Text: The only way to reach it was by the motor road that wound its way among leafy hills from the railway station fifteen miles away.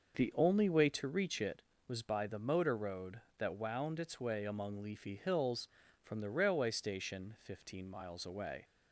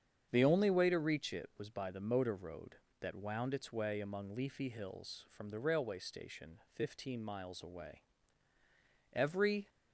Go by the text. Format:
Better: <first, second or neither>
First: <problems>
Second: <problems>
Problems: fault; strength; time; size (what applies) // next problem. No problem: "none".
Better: first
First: starts louder than the rest; noticeable; until 1.2 s; 6 dB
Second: starts louder than the rest; strong; until 1.3 s; 8 dB // pauses between "station" and "fifteen"; slight; at 6.5 s; 0.16 s long // goes on to say "Every"; from 9.1 s on; 0.58 s long